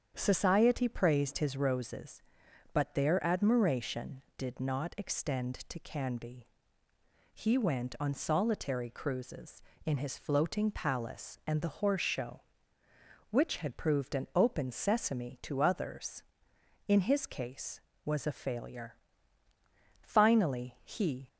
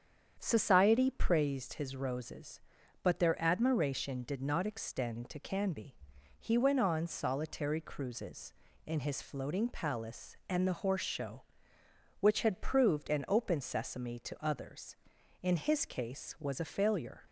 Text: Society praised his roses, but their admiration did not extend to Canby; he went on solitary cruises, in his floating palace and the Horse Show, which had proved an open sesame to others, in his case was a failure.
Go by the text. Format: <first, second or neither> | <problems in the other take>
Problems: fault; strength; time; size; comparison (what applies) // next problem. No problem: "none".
second | starts louder than the rest; strong; until 1.1 s; 8 dB; strong in the second // goes on to say "Finally he"; noticeable; from 20.0 s on; 1.2 s long